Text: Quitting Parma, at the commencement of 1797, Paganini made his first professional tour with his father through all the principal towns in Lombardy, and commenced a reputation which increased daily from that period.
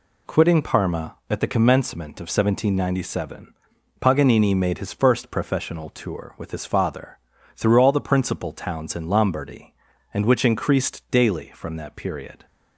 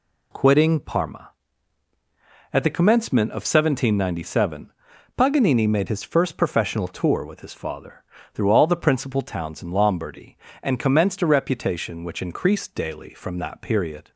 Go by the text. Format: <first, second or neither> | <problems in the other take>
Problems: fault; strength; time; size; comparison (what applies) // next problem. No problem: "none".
second | pauses between "father" and "through"; slight; at 7.1 s; 0.36 s long; slight in the second // skips "commenced a reputation"; at 10.2 s